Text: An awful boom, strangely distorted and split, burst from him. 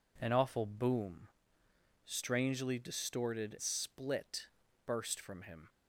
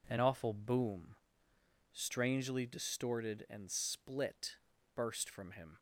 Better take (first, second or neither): second